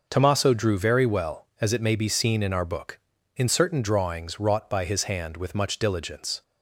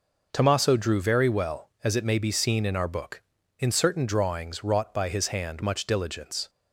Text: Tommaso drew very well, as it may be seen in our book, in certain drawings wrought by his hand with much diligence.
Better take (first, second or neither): first